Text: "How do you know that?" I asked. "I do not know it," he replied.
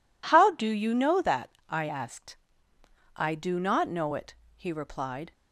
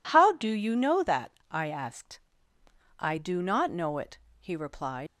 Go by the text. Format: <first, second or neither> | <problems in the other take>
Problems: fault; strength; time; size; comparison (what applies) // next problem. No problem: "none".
first | leaves "replied" unfinished; at 5.0 s; 85 ms